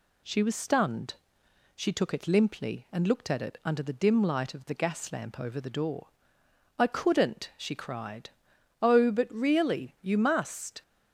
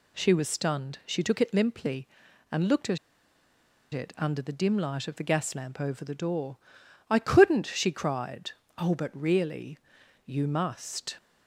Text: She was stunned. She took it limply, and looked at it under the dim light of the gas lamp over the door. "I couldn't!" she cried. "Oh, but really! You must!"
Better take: first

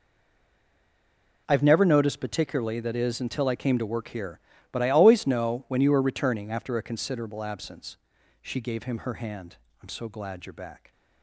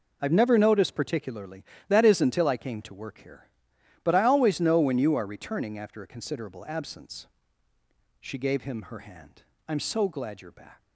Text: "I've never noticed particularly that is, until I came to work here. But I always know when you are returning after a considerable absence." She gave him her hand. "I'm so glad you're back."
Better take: second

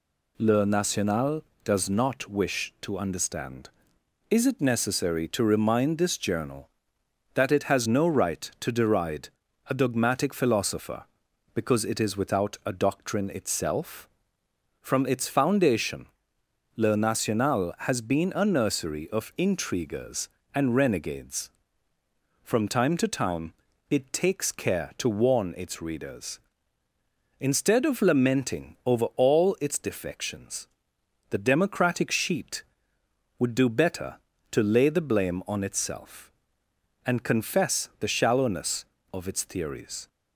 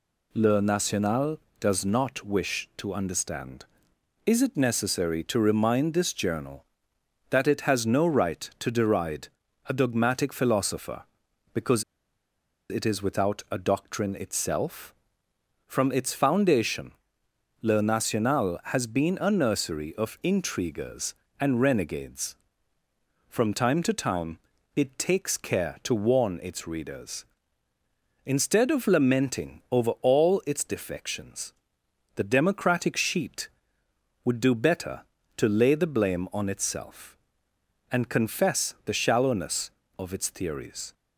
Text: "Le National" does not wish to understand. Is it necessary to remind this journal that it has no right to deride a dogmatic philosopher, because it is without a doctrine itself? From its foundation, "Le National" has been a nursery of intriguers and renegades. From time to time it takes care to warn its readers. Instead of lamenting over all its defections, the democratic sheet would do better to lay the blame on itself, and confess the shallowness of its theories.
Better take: first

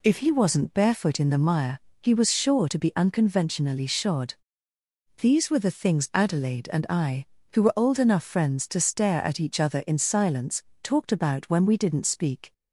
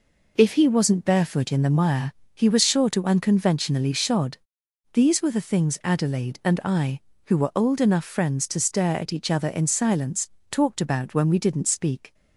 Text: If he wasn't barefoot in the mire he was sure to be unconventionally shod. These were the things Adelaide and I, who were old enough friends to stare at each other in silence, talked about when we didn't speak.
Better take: first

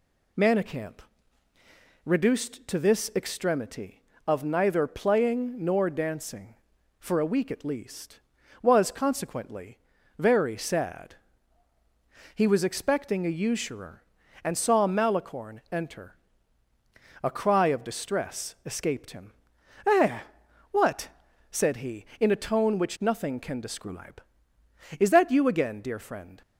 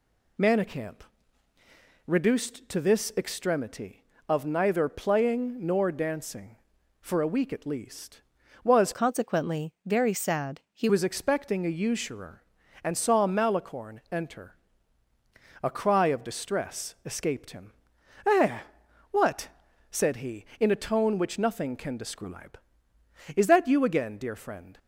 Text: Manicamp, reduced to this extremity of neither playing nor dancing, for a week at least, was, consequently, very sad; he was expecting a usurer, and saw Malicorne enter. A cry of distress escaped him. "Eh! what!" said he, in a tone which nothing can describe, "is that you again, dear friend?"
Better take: first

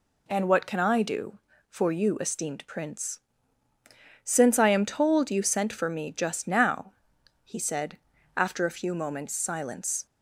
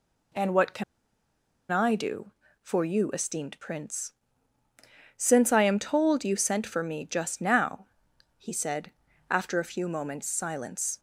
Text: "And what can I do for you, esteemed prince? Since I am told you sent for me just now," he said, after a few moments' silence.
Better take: first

